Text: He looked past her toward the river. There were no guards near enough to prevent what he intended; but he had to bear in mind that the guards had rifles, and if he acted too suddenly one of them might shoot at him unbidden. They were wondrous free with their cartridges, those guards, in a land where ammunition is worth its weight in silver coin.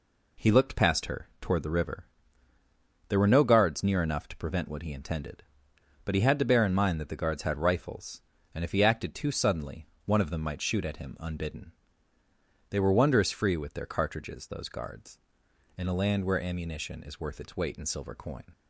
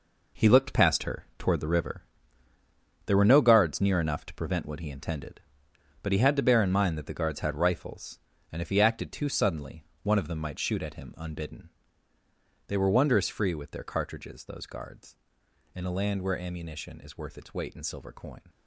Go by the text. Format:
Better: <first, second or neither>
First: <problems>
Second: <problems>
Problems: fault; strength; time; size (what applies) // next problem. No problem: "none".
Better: first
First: pauses between "suddenly" and "one"; slight; at 9.8 s; 0.20 s long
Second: gets quieter; strong; throughout; 10 dB // pauses between "suddenly" and "one"; slight; at 9.8 s; 0.20 s long